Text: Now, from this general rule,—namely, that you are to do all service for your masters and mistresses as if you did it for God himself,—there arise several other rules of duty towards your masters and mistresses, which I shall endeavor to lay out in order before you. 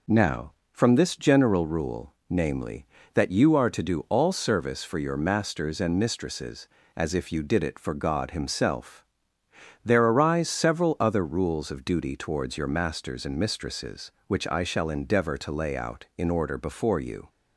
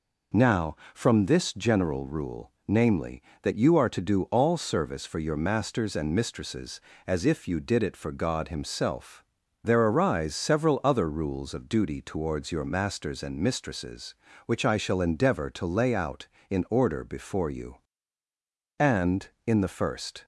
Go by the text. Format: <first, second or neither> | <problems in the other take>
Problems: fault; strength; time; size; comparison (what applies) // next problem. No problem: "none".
first | goes on to say "And in the first"; from 18.8 s on; 1.4 s long